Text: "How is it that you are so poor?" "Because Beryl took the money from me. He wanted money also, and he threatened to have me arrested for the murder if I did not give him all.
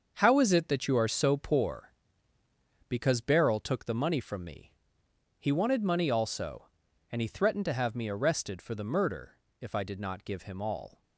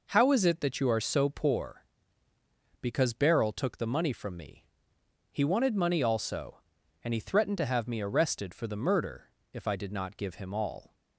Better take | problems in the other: second | gets quieter; strong; throughout; 9 dB // pauses between "murder" and "if"; slight; at 9.3 s; 0.22 s long; slight in the second

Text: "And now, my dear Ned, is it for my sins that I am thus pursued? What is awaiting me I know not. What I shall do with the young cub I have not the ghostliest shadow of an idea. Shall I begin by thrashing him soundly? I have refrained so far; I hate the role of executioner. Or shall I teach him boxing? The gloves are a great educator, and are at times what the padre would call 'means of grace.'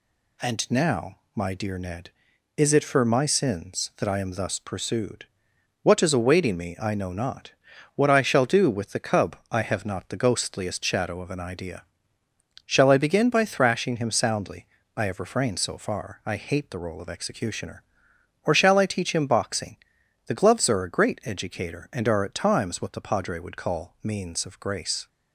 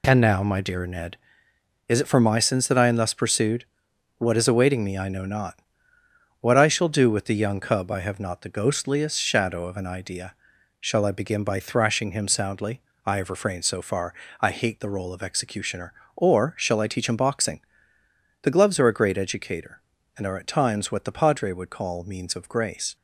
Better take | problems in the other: second | skips "young"; at 9.0 s

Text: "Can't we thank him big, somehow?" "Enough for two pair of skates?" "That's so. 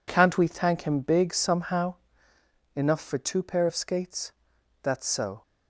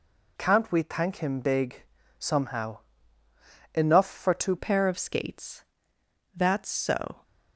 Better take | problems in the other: first | changes voice at "pair"; from 4.5 s on; 2.7 s long

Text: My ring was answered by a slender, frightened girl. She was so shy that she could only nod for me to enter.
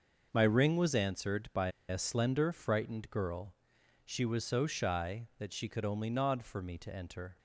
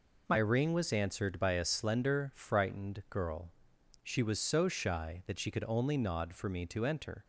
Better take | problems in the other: second | starts louder than the rest; noticeable; until 1.3 s; 6 dB // pauses between "by" and "a"; slight; at 1.6 s; 0.18 s long

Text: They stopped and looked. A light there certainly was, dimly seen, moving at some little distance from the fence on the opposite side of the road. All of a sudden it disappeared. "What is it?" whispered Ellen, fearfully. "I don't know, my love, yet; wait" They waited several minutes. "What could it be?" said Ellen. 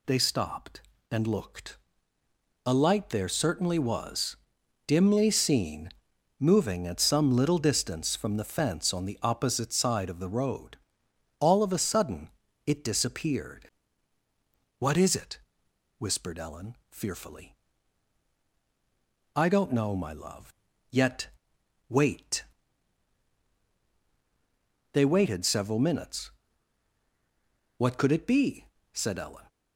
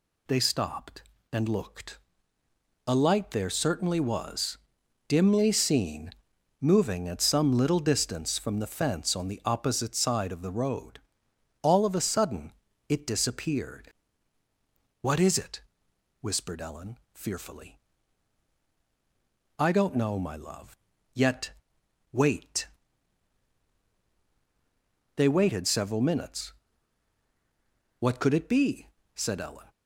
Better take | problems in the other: neither | pauses between "sudden" and "it"; slight; the same in both // pauses between "wait" and "They"; strong; the same in both

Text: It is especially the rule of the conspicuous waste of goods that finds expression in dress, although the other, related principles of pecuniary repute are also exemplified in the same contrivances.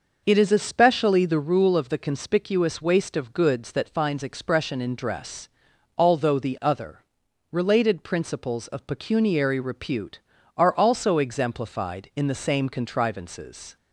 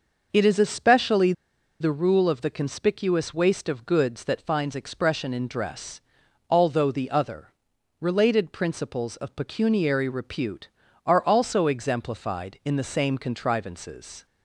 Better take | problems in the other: first | pauses between "especially" and "the"; noticeable; at 1.3 s; 0.48 s long

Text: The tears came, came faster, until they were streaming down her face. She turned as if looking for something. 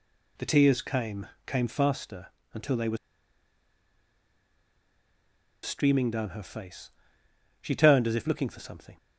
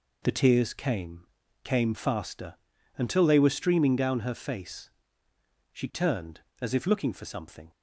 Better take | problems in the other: second | pauses between "were" and "streaming"; strong; at 2.9 s; 2.6 s long

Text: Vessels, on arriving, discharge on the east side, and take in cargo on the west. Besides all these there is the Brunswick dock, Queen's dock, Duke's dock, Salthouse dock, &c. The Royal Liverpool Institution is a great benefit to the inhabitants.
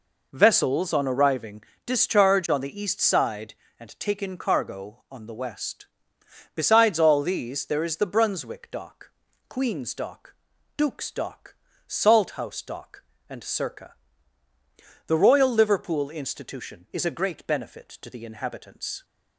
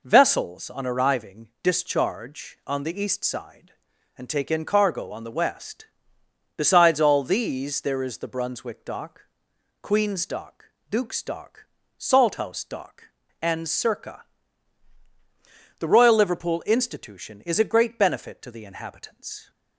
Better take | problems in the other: neither | none

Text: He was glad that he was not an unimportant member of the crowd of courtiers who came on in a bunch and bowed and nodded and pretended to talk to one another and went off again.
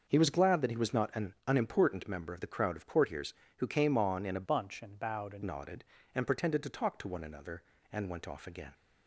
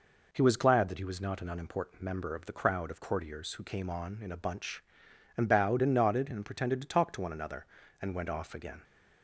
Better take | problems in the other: second | starts louder than the rest; noticeable; until 1.0 s; 6 dB // changes voice from "bunch" to "and"; from 4.4 to 5.4 s; 1.0 s long

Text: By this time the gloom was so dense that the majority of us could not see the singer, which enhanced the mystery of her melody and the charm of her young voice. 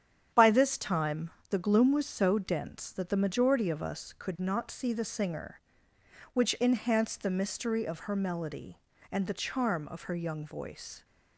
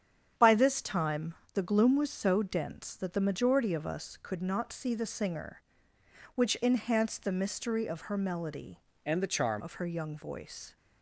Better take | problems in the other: first | starts louder than the rest; strong; until 1.6 s; 8.5 dB; strong in the first // pauses between "time" and "the"; slight; at 1.3 s; 0.22 s long; slight in the first // changes voice from "and" to "charm"; from 9.0 to 9.6 s; 0.6 s long

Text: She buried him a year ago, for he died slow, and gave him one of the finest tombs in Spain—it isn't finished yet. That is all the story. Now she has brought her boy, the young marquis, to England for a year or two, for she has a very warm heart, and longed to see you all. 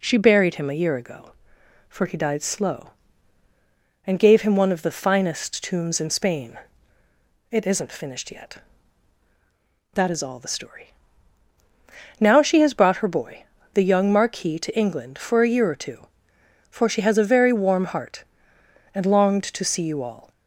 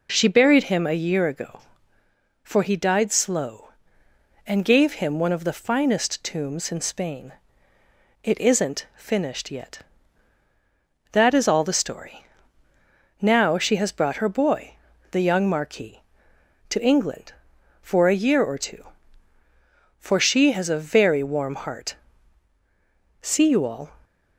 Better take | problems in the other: first | skips "and longed to"; at 22.5 s

